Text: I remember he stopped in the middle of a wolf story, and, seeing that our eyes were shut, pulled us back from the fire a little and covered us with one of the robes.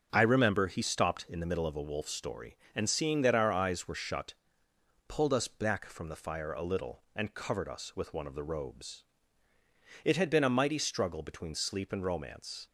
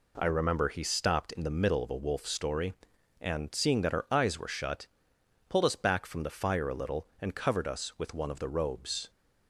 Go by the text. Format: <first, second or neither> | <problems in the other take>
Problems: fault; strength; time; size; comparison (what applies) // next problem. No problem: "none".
second | starts louder than the rest; until 1.1 s; 7 dB // goes on to say "It had been a mighty struggle between Sleep and Romance"; strong; from 10.0 s on; 2.6 s long